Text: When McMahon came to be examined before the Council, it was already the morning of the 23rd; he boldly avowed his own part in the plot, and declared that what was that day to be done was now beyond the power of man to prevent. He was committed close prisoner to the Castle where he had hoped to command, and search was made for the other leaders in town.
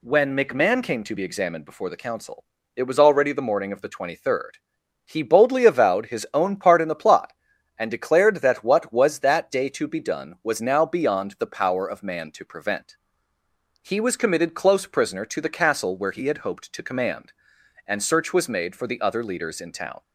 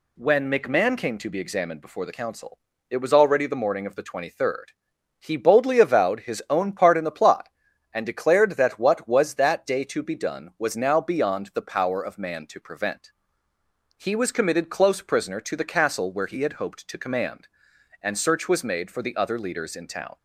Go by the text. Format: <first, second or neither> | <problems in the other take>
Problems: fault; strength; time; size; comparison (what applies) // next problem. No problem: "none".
neither | none